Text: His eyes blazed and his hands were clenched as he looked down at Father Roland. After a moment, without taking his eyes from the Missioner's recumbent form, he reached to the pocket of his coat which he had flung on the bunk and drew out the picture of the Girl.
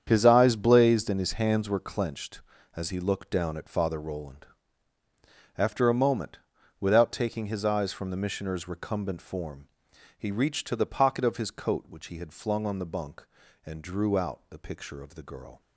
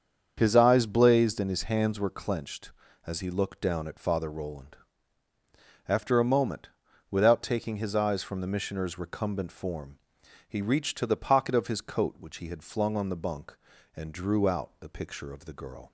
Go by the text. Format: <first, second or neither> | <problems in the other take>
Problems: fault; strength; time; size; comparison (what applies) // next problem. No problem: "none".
second | gets quieter; strong; throughout; 12 dB // starts louder than the rest; strong; until 1.0 s; 8.5 dB; strong in the second